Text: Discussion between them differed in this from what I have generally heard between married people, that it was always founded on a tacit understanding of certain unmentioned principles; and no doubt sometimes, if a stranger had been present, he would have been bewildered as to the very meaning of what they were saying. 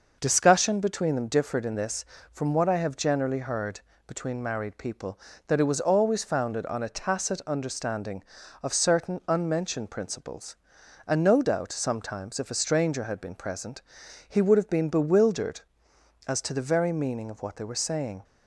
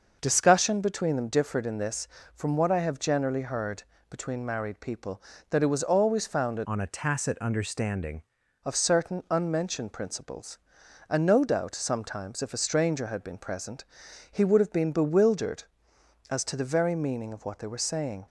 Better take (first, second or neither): first